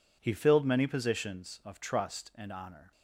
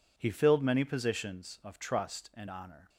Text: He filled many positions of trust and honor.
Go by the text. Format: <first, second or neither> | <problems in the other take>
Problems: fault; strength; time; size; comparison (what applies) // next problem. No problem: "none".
neither | none